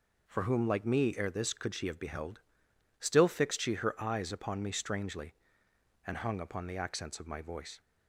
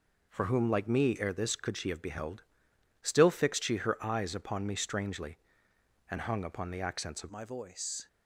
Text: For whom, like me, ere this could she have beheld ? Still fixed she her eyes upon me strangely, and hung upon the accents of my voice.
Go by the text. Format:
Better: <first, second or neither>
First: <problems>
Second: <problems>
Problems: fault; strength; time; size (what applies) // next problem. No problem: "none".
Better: first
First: none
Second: changes voice at "my"; from 7.3 s on; 0.7 s long